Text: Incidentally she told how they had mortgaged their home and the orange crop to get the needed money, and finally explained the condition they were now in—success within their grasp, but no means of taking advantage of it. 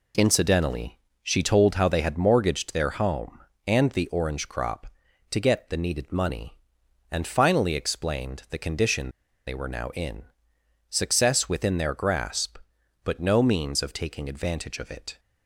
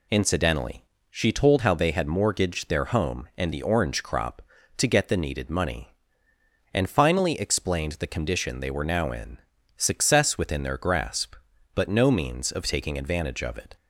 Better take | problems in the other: second | pauses between "Incidentally" and "she"; slight; at 0.9 s; 0.24 s long; slight in the second // pauses between "condition" and "they"; at 9.0 s; 0.36 s long

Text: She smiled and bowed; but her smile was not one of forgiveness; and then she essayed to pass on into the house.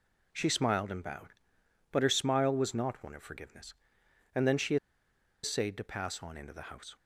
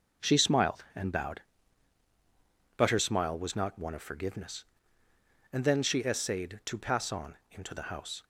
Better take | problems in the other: second | pauses between "she" and "essayed"; noticeable; at 4.7 s; 0.67 s long

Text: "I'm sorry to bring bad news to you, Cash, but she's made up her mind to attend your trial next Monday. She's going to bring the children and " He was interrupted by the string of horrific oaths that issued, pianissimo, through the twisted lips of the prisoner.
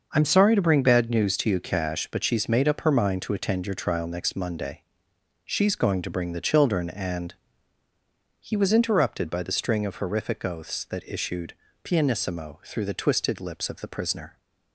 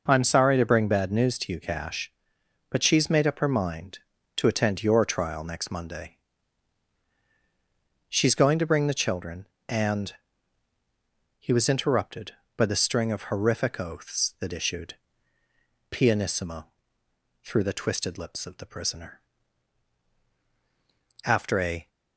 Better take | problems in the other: first | starts louder than the rest; noticeable; until 1.0 s; 6 dB; also in the first // goes on to say "After a"; noticeable; from 21.2 s on; 0.64 s long

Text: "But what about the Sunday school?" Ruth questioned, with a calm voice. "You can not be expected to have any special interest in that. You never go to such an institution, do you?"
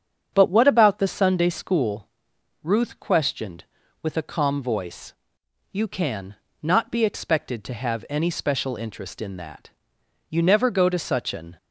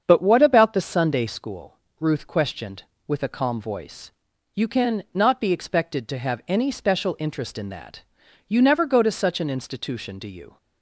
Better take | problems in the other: second | starts louder than the rest; strong; until 1.3 s; 7.5 dB; strong in the second // pauses between "can" and "not"; slight; at 6.3 s; 0.26 s long // stops before "institution do you"; at 11.5 s

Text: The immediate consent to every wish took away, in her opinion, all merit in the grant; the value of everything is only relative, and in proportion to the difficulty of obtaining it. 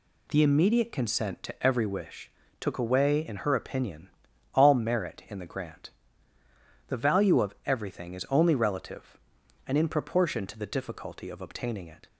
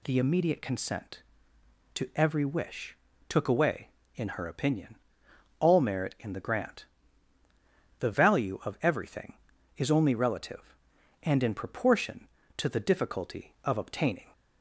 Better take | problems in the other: first | pauses between "wish" and "took"; slight; at 2.9 s; 0.34 s long; slight in the first // stops before "it"; at 14.3 s

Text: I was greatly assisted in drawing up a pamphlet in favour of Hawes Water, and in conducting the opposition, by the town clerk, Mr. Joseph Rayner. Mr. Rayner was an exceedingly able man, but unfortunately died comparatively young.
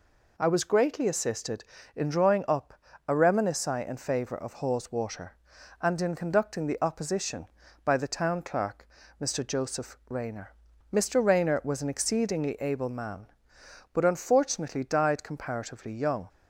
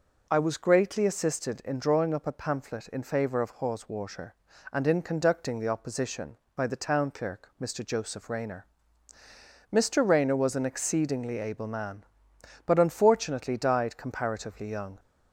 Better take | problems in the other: second | pauses between "up" and "a"; slight; at 2.7 s; 0.34 s long // says "reminisci" for "pamphlet"; at 3.1 s

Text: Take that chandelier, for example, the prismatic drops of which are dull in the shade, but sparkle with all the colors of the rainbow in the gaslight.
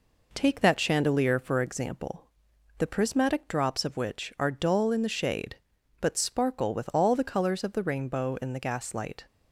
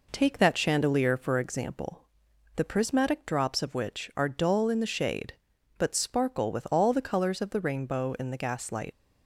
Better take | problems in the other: first | leaves "gaslight" unfinished; at 8.9 s; 110 ms

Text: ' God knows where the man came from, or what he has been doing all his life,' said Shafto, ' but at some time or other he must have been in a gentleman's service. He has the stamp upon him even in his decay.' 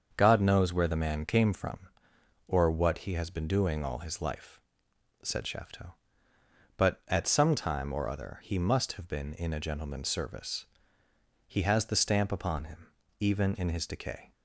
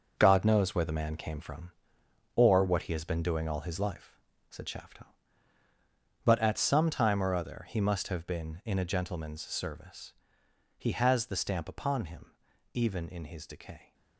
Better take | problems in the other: first | gets quieter; strong; throughout; 7.5 dB // starts louder than the rest; noticeable; until 1.1 s; 6 dB; also in the first // pauses between "him" and "even"; at 12.3 s; 0.42 s long; slight in the first

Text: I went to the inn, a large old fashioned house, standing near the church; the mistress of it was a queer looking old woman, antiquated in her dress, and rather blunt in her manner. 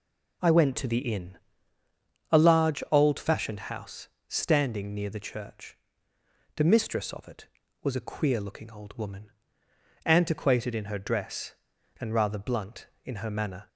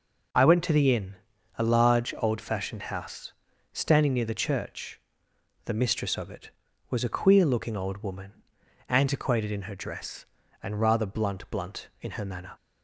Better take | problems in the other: first | says "blunt" twice; at 11.5 s

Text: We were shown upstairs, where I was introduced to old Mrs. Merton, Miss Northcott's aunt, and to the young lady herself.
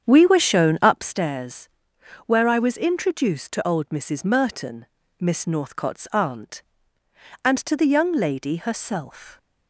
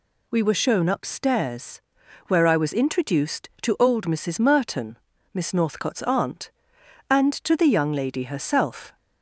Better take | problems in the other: second | starts louder than the rest; strong; until 1.1 s; 8 dB

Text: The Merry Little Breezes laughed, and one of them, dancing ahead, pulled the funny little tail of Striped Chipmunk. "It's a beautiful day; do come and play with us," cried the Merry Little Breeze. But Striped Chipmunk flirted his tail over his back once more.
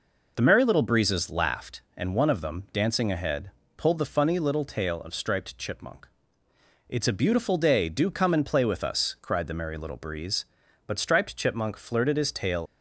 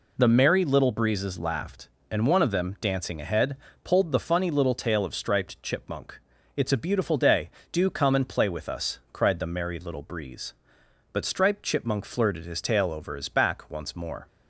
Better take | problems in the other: second | stops before "over his back once more"; at 12.6 s

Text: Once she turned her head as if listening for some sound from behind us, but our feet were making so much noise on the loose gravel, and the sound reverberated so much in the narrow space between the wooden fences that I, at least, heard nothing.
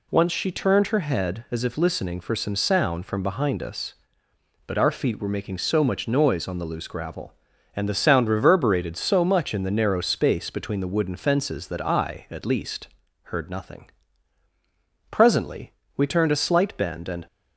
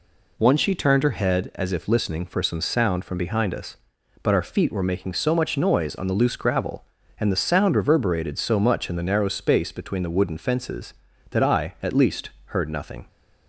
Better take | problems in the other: second | goes on to say "Presently we turned a slight bend and"; strong; from 15.1 s on; 2.1 s long

